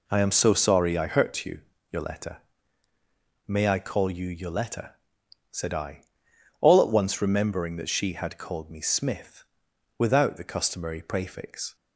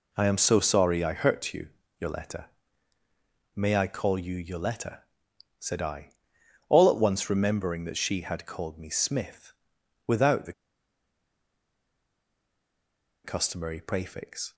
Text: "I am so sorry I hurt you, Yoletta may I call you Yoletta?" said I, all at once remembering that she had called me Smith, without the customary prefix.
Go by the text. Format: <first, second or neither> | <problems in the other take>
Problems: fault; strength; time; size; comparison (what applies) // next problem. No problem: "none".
first | pauses between "Yoletta" and "may"; at 2.4 s; 1.0 s long; also in the first // pauses between "the" and "customary"; strong; at 10.5 s; 2.7 s long